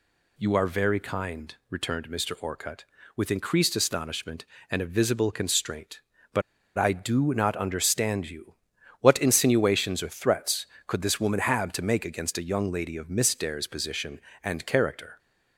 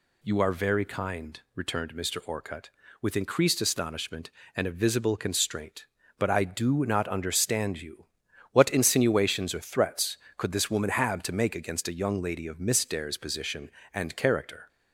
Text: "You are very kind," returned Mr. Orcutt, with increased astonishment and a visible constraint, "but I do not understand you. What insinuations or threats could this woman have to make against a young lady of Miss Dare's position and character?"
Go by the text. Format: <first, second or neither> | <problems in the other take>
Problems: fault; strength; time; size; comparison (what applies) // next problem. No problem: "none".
second | pauses between "but" and "I"; slight; at 6.4 s; 0.36 s long